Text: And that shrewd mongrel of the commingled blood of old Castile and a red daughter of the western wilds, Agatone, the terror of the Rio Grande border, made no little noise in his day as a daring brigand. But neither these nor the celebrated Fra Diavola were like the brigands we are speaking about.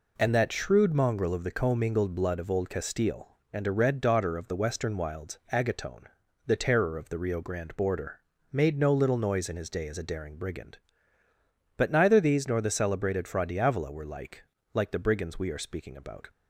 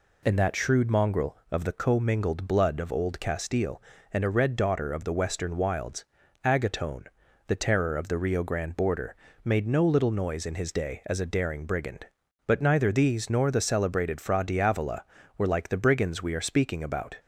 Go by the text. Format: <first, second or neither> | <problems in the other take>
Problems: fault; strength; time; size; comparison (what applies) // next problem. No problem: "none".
second | says "like" twice; at 14.7 s